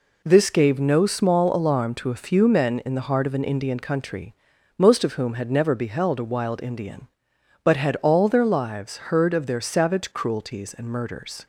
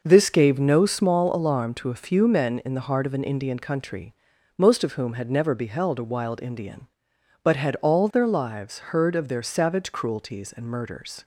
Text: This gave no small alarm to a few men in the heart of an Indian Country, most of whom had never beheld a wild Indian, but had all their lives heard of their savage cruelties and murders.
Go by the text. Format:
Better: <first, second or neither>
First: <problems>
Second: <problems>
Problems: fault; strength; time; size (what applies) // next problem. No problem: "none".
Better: first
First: none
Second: starts louder than the rest; noticeable; until 1.1 s; 5.5 dB